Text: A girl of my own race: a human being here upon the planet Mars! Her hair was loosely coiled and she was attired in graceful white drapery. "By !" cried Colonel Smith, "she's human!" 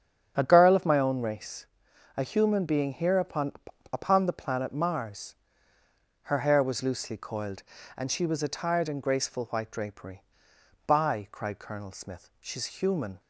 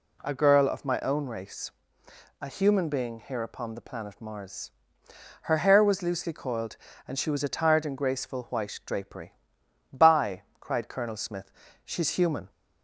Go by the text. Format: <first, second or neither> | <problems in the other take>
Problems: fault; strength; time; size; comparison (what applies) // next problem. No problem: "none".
second | starts louder than the rest; strong; until 1.3 s; 8 dB // says "upon" twice; at 3.9 s